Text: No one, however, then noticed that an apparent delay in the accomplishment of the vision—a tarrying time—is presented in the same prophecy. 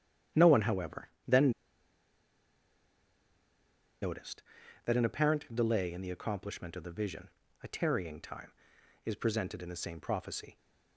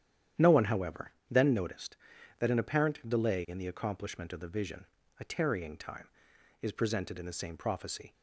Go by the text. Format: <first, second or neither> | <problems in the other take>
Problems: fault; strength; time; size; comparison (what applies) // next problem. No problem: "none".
second | starts louder than the rest; strong; until 4.0 s; 10 dB; strong in the second // pauses between "then" and "noticed"; strong; at 1.5 s; 2.5 s long